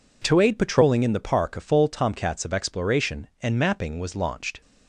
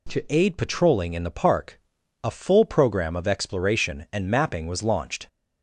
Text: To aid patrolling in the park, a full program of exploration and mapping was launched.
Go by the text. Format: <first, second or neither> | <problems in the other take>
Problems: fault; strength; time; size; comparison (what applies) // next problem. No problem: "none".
second | says "tomcats" for "program"; at 1.8 s